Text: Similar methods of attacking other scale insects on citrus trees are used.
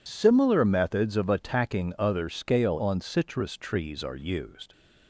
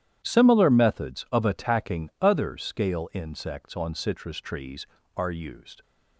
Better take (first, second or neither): second